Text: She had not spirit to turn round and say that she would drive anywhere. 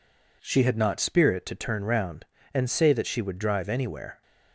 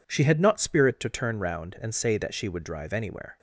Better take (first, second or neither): neither